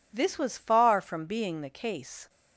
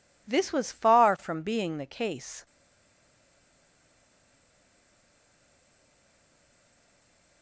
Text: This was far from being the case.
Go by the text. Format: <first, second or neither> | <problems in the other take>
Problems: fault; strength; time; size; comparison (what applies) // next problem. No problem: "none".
first | stays silent after the last word; strong; from 2.4 s on; 5.0 s long